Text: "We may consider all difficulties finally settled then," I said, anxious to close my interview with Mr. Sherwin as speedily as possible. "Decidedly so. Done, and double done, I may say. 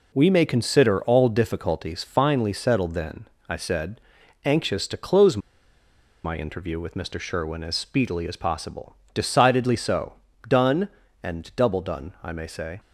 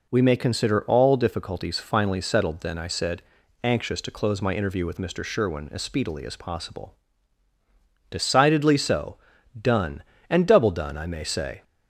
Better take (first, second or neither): second